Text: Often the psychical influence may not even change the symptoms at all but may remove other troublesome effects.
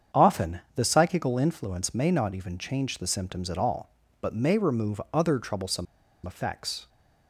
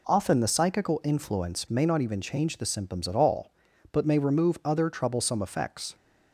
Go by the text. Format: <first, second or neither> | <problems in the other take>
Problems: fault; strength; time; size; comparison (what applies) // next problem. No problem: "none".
second | starts louder than the rest; strong; until 1.2 s; 7.5 dB // pauses between "troublesome" and "effects"; at 5.8 s; 0.41 s long